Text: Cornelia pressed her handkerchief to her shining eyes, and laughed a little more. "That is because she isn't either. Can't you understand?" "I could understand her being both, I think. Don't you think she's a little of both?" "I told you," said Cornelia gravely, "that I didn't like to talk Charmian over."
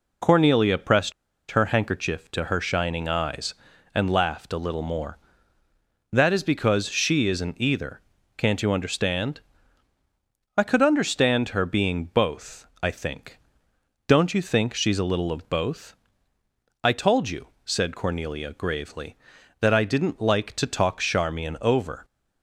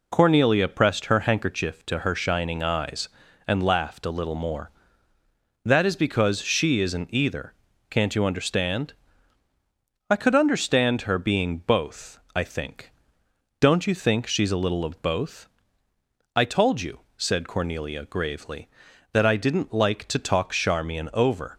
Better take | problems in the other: second | pauses between "pressed" and "her"; at 1.1 s; 0.38 s long

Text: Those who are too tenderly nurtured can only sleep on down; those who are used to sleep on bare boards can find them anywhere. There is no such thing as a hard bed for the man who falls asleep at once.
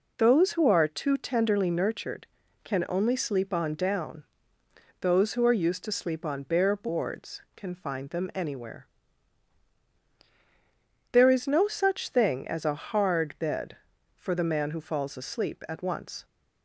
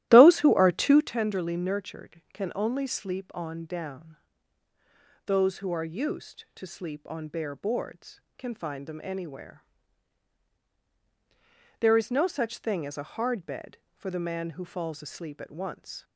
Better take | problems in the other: first | starts louder than the rest; strong; until 1.2 s; 15 dB

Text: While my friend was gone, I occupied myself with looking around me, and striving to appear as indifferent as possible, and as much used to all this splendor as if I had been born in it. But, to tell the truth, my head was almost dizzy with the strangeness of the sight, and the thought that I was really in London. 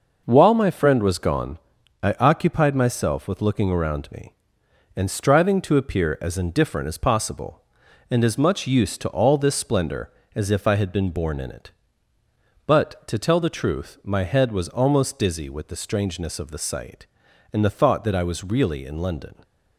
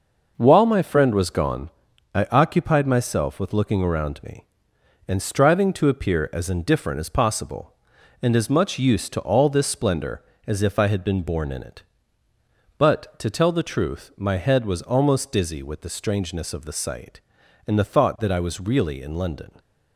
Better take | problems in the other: neither | none

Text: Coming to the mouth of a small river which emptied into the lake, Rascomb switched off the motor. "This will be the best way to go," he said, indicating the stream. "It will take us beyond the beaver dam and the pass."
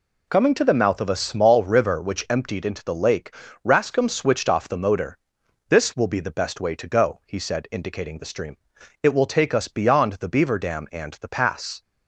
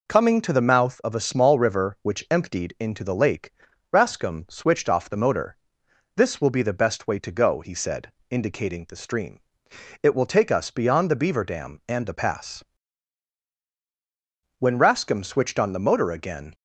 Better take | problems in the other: first | goes on to say "When Rascomb switched on the motor again"; strong; from 14.5 s on; 1.9 s long

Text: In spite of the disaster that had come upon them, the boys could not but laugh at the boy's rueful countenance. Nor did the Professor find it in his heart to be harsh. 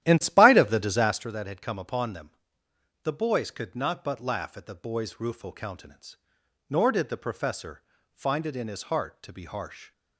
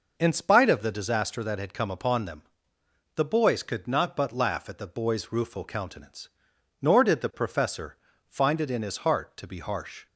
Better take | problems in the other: second | starts louder than the rest; strong; until 1.3 s; 12.5 dB // pauses between "Professor" and "find"; slight; at 7.8 s; 0.32 s long; slight in the second

